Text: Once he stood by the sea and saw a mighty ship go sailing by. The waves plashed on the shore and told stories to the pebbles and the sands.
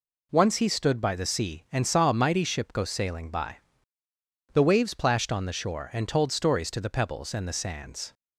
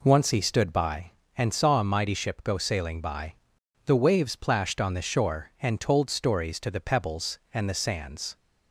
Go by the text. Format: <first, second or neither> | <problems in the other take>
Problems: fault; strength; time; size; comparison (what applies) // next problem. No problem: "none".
first | skips "the sea"; at 1.2 s